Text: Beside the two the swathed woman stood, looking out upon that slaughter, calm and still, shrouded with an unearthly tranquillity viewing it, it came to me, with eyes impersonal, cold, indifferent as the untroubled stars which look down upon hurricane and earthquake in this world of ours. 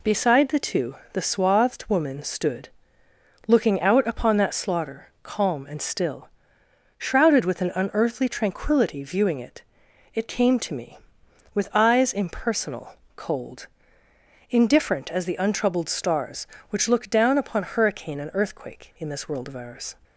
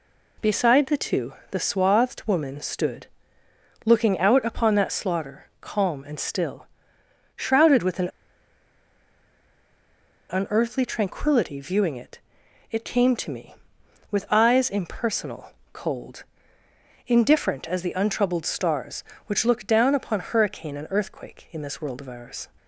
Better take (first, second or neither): first